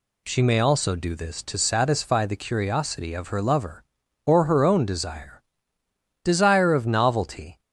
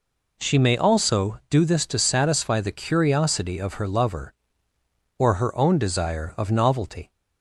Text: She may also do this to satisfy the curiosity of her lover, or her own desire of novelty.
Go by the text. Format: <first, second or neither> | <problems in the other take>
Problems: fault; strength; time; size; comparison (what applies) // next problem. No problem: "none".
second | says "desire" twice; at 6.2 s